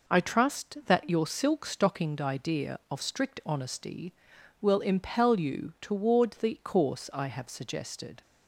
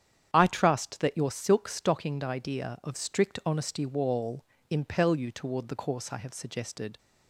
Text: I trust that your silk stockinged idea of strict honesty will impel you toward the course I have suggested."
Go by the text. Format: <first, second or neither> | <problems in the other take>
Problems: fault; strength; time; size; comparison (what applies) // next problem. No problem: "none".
first | starts louder than the rest; strong; until 1.3 s; 9 dB // says "wall" for "will"; at 3.8 s